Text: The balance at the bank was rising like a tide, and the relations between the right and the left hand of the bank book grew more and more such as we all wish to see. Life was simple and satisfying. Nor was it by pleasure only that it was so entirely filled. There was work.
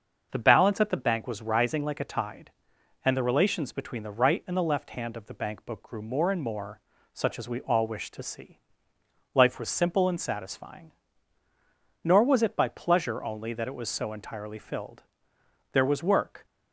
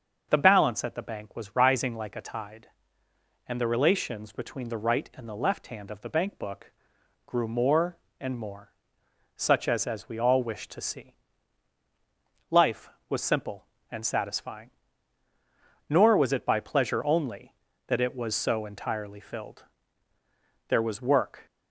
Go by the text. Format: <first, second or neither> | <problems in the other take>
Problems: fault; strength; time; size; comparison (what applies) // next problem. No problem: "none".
first | starts louder than the rest; until 1.3 s; 6 dB; also in the first // pauses between "book" and "grew"; noticeable; at 6.7 s; 0.54 s long // pauses between "more" and "such"; noticeable; at 8.7 s; 0.64 s long; slight in the first // says "as" twice; at 9.8 s